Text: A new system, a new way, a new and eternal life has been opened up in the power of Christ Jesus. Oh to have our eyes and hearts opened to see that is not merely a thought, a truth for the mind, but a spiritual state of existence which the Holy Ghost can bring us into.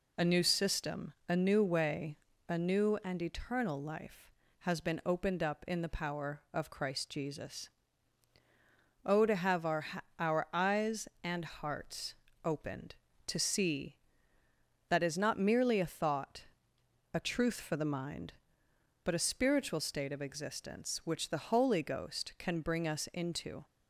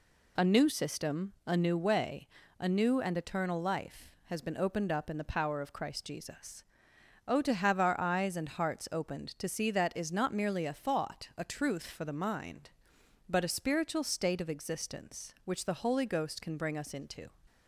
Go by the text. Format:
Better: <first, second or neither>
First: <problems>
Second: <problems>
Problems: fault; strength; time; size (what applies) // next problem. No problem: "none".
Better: second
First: says "our" twice; at 10.1 s // pauses between "hearts" and "opened"; slight; at 12.1 s; 0.32 s long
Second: none